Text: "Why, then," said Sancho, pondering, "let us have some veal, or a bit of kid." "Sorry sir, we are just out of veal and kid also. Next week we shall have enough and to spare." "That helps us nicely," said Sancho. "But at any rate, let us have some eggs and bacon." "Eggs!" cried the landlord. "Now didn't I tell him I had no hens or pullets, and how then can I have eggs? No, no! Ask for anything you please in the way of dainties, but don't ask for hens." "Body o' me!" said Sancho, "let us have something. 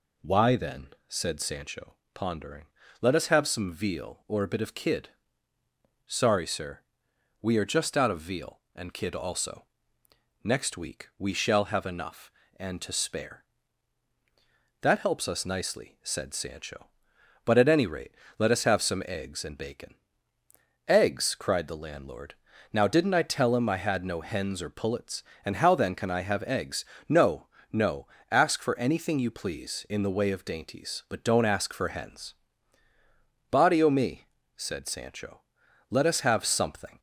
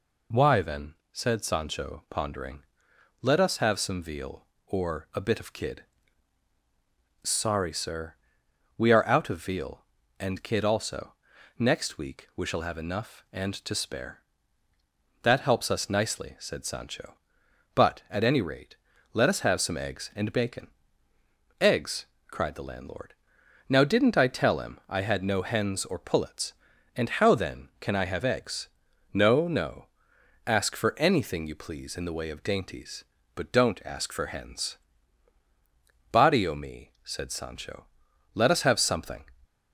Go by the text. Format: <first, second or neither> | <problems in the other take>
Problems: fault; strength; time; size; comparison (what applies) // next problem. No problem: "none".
first | skips "just"; at 9.0 s